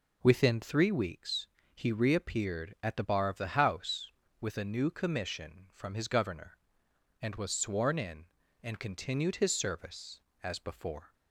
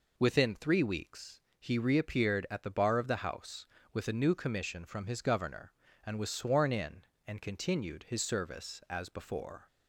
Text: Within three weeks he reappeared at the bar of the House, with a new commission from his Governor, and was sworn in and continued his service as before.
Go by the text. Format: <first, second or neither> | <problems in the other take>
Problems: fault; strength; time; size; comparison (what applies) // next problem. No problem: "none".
neither | pauses between "weeks" and "he"; slight; the same in both